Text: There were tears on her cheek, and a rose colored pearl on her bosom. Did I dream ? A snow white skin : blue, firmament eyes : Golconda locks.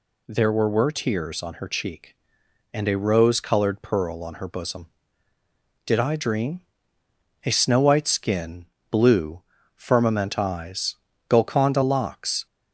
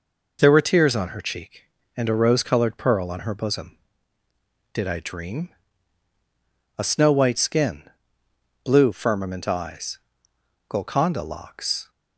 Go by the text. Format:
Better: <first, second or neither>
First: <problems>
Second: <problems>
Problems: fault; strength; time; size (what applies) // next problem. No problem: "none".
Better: second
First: says "were" twice; at 0.6 s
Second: none